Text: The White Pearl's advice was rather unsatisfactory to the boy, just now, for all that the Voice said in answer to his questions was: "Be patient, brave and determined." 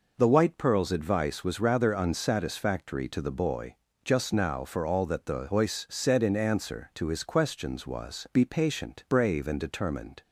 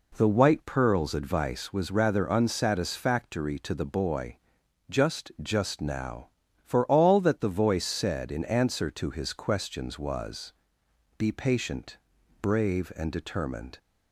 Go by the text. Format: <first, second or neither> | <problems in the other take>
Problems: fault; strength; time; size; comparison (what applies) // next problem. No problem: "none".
first | says "just" twice; at 5.4 s